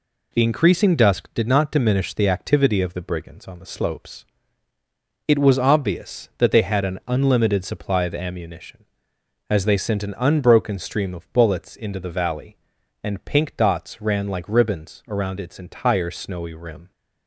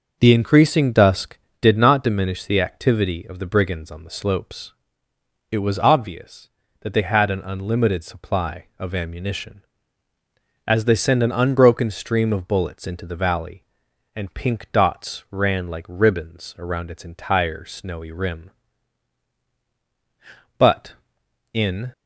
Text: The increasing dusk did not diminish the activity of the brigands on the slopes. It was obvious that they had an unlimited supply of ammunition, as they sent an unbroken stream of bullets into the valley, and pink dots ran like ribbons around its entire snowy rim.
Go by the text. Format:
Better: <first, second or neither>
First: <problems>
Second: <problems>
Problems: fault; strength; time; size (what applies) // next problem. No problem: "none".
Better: first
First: none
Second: goes on to say "But in"; from 20.5 s on; 1.3 s long